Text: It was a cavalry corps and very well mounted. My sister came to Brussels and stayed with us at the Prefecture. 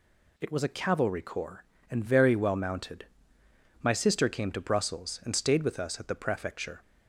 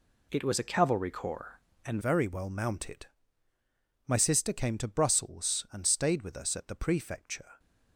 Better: first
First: none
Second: changes voice at "very"; from 2.0 s on; 5.5 s long

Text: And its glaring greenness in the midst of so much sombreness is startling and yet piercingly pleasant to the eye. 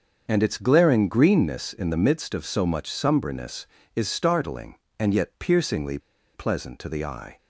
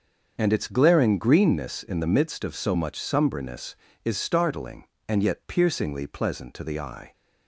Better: second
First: starts louder than the rest; until 1.2 s; 6.5 dB // pauses between "piercingly" and "pleasant"; slight; at 5.9 s; 0.35 s long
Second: starts louder than the rest; until 1.3 s; 6.5 dB

